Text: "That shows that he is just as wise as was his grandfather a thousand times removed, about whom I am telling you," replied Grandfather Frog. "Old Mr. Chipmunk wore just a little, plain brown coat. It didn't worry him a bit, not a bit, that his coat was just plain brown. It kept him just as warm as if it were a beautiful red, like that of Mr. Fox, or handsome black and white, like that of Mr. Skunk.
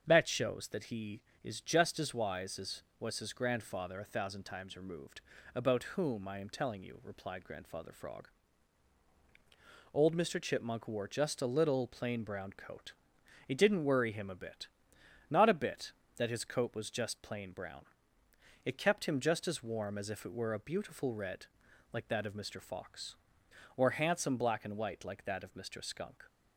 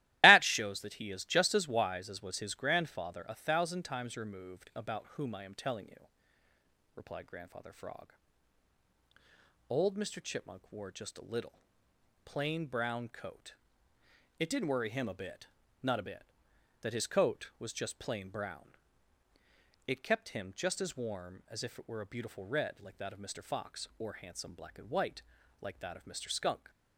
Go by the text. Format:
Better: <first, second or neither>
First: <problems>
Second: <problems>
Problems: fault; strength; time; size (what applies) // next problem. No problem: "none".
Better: first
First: starts louder than the rest; strong; until 1.0 s; 7.5 dB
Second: loses the start of "That"; at 0.2 s; 80 ms // starts louder than the rest; strong; until 1.2 s; 16 dB